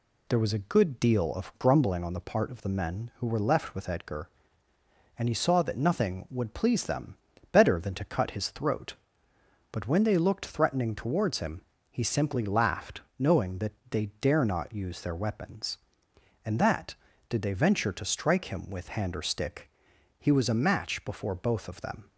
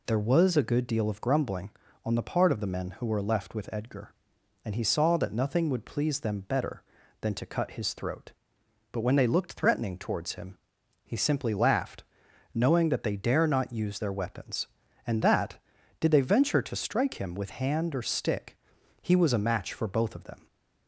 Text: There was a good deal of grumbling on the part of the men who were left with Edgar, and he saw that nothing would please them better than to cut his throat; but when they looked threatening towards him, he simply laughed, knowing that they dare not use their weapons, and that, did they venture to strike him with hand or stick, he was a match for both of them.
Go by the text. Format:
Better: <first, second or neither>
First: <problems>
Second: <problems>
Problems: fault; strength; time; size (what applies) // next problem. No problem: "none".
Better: second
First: pauses between "them" and "better"; at 7.1 s; 0.38 s long // pauses between "that" and "they"; slight; at 13.7 s; 0.20 s long // says "before" for "for"; at 21.0 s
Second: none